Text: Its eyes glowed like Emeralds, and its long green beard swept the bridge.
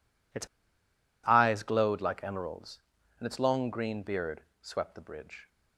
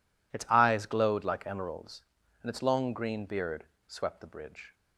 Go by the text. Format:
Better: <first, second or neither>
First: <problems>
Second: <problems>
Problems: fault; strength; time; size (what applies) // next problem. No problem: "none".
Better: second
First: pauses between "Its" and "eyes"; noticeable; at 0.4 s; 0.77 s long // pauses between "beard" and "swept"; slight; at 4.4 s; 0.18 s long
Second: pauses between "beard" and "swept"; slight; at 3.6 s; 0.20 s long